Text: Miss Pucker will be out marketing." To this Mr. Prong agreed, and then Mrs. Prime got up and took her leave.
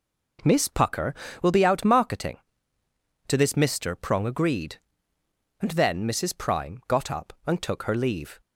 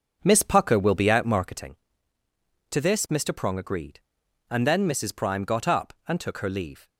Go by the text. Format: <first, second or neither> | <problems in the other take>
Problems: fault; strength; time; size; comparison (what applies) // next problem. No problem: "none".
first | starts louder than the rest; strong; until 1.7 s; 7.5 dB